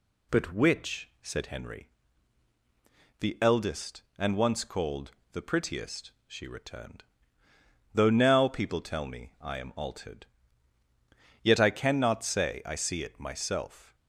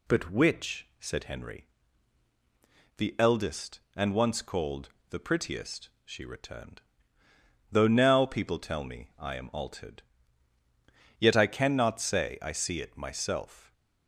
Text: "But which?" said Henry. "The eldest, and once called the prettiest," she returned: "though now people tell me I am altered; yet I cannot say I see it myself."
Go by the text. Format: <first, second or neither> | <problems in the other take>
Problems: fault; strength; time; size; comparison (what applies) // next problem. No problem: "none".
neither | pauses between "called" and "the"; slight; the same in both